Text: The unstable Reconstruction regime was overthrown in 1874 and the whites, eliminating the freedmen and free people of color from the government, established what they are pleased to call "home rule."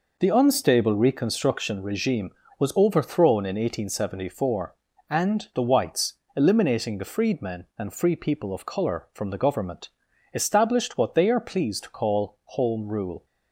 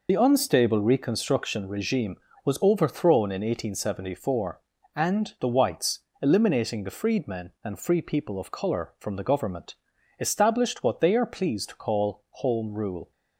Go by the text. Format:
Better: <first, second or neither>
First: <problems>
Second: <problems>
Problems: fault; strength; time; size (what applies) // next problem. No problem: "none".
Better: first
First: none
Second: loses the start of "The"; at 0.0 s; 45 ms